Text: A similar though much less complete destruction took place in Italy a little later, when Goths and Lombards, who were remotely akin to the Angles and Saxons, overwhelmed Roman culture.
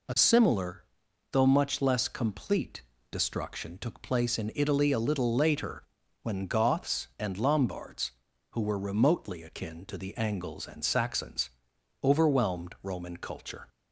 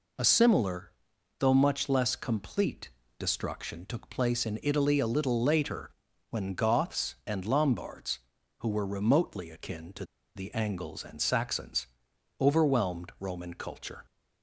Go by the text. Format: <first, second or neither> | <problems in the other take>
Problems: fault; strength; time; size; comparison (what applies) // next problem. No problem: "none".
first | pauses between "similar" and "though"; noticeable; at 0.9 s; 0.46 s long; noticeable in the first // pauses between "complete" and "destruction"; slight; at 2.8 s; 0.28 s long; slight in the first // pauses between "to" and "the"; slight; at 10.0 s; 0.31 s long